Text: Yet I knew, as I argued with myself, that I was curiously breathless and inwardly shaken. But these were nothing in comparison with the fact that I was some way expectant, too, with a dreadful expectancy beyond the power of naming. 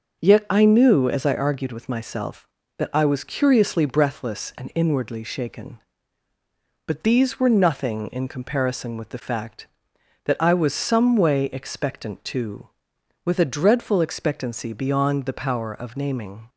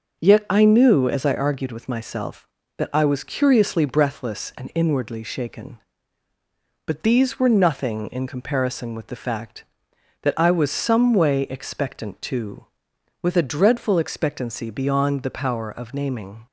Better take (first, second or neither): neither